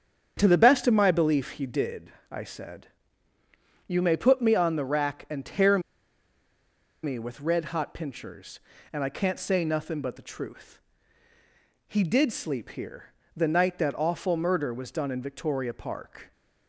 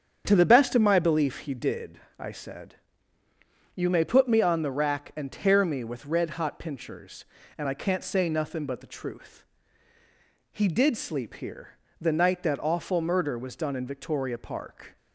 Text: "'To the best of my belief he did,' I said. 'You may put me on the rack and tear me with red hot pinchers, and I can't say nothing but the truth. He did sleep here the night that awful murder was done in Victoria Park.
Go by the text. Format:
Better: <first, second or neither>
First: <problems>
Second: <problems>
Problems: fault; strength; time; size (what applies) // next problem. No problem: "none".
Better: second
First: starts louder than the rest; strong; until 1.3 s; 8 dB // pauses between "tear" and "me"; at 5.8 s; 1.2 s long // pauses between "here" and "the"; slight; at 13.0 s; 0.30 s long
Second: starts louder than the rest; strong; until 1.2 s; 8 dB // pauses between "here" and "the"; slight; at 11.6 s; 0.30 s long